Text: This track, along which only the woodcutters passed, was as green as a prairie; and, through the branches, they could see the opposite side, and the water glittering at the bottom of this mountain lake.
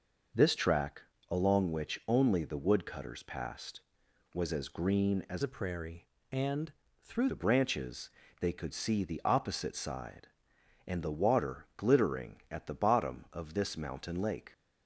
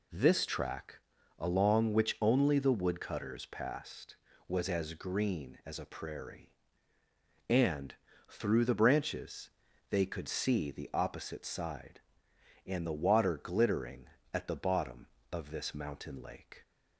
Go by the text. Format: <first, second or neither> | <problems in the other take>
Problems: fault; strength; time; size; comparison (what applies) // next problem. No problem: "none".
second | changes voice from "a" to "through"; from 5.4 to 7.2 s; 1.8 s long